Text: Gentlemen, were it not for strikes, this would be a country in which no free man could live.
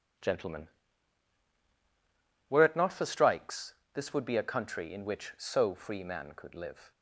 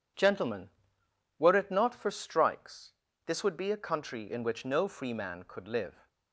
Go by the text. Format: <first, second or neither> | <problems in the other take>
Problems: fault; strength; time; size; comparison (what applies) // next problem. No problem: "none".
second | says "so" for "no"; at 5.3 s